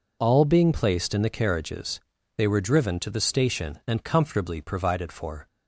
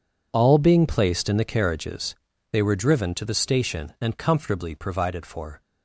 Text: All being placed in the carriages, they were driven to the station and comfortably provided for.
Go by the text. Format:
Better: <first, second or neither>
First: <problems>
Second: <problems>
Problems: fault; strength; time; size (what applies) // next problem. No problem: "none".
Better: first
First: none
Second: gets quieter; strong; throughout; 14 dB